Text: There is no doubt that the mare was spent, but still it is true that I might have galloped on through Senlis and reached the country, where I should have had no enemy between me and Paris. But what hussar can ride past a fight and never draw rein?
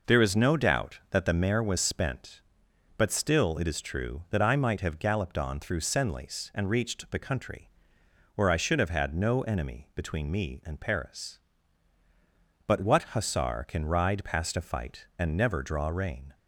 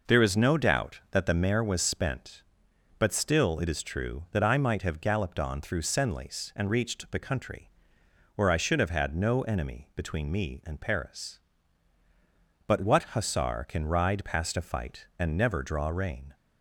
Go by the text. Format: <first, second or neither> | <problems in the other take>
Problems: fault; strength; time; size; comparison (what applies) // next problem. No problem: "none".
neither | none